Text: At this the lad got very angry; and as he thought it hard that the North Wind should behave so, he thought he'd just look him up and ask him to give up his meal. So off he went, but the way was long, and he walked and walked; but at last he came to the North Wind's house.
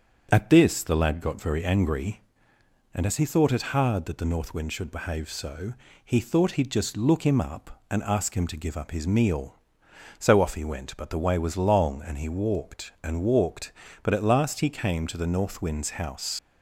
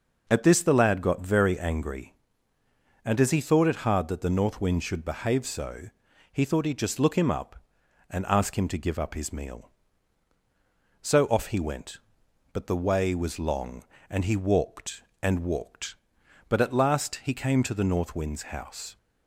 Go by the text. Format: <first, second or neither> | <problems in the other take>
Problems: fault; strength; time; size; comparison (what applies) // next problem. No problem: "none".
second | starts louder than the rest; strong; until 1.3 s; 7.5 dB // leaves "house" unfinished; at 16.3 s; 65 ms